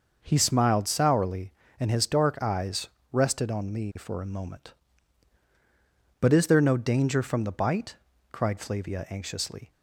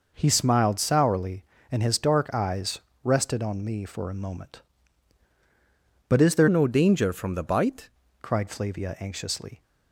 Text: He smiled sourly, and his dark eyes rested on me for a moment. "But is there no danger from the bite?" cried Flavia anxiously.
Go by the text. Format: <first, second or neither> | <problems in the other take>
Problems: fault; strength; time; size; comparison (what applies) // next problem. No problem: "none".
first | pauses between "eyes" and "rested"; slight; at 2.7 s; 0.24 s long; slight in the first // changes voice from "no" to "bite"; from 6.4 to 7.8 s; 1.4 s long